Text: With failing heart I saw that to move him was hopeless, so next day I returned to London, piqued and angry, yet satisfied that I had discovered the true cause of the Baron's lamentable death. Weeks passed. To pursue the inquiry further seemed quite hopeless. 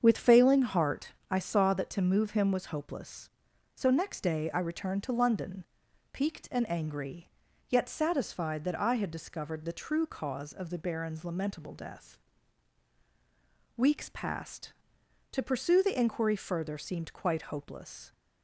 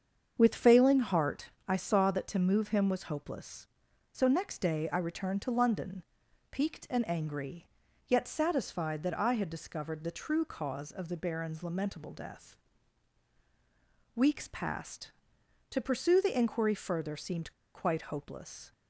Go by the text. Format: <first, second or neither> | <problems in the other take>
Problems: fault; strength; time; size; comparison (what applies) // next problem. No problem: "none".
first | starts louder than the rest; strong; until 1.3 s; 7 dB; strong in the first // pauses between "heart" and "I"; slight; at 1.4 s; 0.18 s long; slight in the first // pauses between "seemed" and "quite"; slight; at 17.5 s; 0.23 s long